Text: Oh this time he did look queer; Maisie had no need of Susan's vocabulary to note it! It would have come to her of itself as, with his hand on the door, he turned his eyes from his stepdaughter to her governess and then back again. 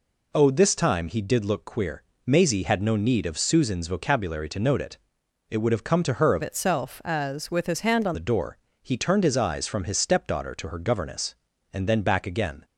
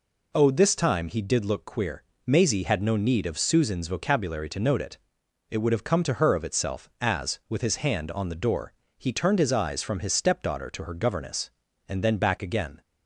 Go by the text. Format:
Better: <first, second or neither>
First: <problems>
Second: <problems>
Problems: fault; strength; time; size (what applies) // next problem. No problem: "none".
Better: second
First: changes voice from "itself" to "on"; from 6.4 to 8.1 s; 1.7 s long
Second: none